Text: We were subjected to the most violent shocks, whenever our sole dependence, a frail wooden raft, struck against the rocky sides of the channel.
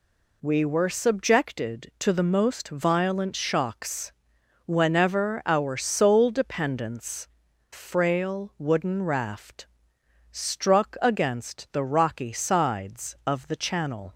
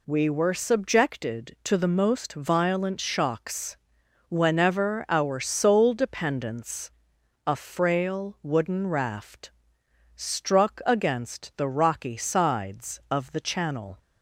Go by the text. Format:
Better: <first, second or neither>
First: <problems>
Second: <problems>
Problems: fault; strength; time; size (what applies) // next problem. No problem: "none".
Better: second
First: skips "a"; at 7.5 s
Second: none